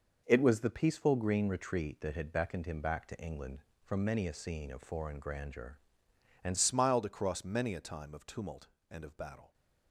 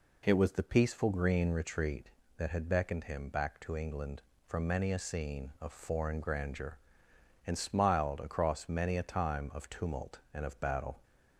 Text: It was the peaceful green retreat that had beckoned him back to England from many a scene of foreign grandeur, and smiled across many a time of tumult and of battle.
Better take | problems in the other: second | changes voice at "smiled"; from 6.5 s on; 3.0 s long

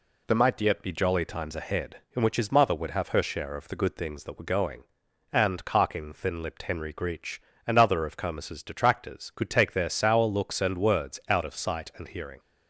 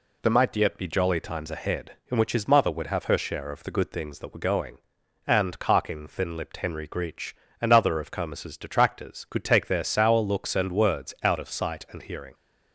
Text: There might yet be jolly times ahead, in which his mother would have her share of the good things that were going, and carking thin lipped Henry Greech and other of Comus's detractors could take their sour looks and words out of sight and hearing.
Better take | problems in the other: neither | none

